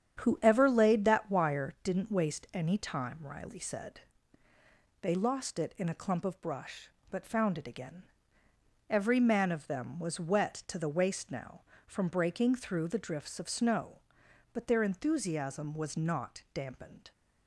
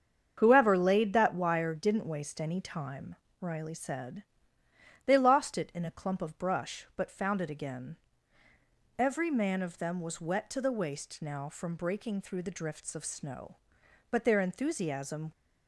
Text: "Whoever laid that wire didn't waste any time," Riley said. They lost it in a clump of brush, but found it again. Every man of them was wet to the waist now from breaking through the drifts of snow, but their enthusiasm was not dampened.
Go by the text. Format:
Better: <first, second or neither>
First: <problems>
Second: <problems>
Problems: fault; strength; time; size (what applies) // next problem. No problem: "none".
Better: first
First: starts louder than the rest; strong; until 1.2 s; 8.5 dB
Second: starts louder than the rest; strong; until 1.3 s; 7.5 dB // stops before "was not dampened"; at 15.3 s